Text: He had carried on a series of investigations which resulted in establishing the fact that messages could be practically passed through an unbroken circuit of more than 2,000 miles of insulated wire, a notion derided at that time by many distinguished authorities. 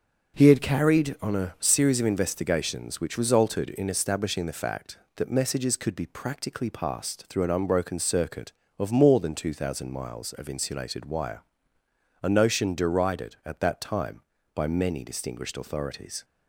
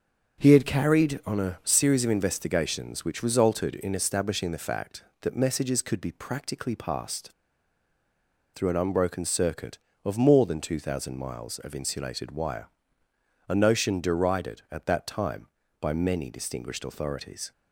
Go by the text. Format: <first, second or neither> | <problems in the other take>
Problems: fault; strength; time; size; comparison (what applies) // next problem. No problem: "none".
first | starts louder than the rest; until 1.4 s; 7 dB; also in the first // pauses between "passed" and "through"; at 7.3 s; 1.2 s long